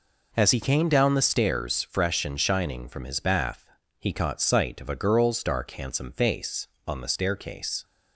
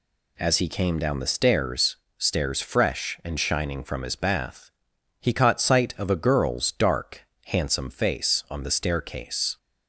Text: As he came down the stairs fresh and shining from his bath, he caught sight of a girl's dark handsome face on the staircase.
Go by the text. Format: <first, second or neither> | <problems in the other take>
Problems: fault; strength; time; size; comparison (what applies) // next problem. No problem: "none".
first | says "stairs" twice; at 2.1 s // pauses between "dark" and "handsome"; slight; at 7.2 s; 0.22 s long